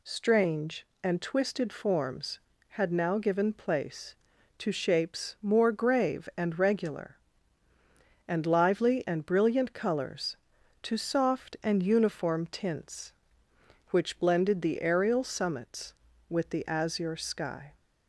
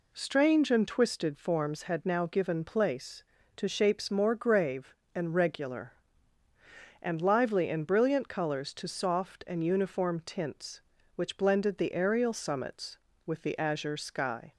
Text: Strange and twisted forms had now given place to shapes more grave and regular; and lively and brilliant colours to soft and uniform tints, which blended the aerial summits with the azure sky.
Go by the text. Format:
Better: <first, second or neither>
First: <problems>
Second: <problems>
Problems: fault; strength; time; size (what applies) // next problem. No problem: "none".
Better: neither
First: none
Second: none